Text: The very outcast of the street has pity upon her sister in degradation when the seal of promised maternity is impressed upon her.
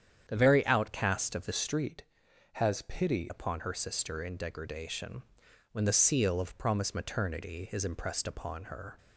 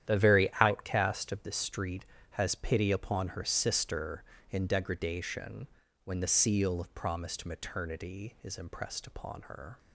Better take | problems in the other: second | starts louder than the rest; strong; until 1.2 s; 8.5 dB; strong in the second // changes voice from "street" to "pity"; from 1.5 to 3.3 s; 1.8 s long // pauses between "degradation" and "when"; noticeable; at 5.2 s; 0.50 s long; also in the second

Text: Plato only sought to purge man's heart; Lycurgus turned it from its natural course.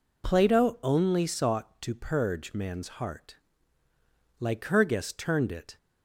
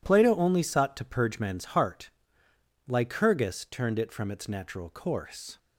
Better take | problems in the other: second | stops before "from its natural course"; at 5.7 s

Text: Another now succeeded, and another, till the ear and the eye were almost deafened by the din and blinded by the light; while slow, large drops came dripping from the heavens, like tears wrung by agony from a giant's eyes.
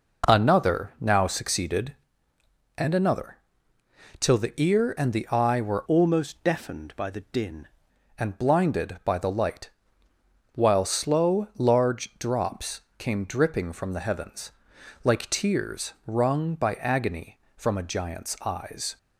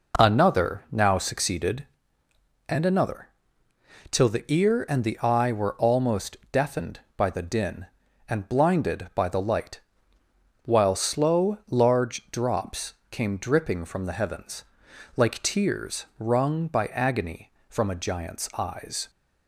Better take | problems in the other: second | changes voice from "almost" to "din"; from 5.8 to 7.6 s; 1.8 s long // pauses between "drops" and "came"; slight; at 12.8 s; 0.18 s long; slight in the second

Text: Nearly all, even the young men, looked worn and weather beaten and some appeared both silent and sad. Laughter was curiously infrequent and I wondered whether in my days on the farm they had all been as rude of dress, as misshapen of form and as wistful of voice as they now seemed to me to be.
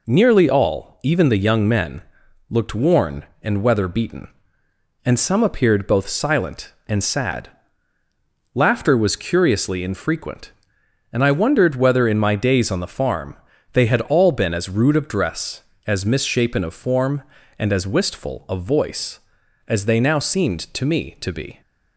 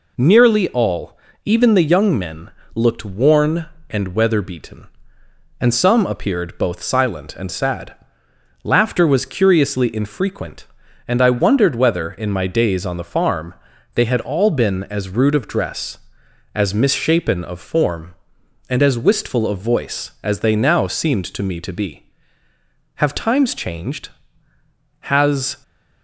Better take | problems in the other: first | pauses between "farm" and "they"; at 13.5 s; 0.40 s long; also in the first // goes on to say "Have times changed Has"; strong; from 22.9 s on; 2.6 s long

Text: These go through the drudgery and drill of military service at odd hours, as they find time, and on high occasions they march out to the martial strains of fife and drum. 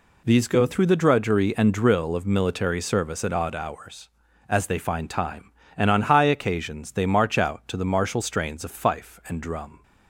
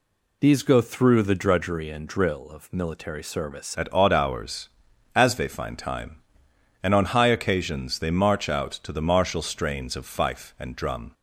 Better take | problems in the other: first | changes voice at "at"; from 3.7 s on; 7.4 s long

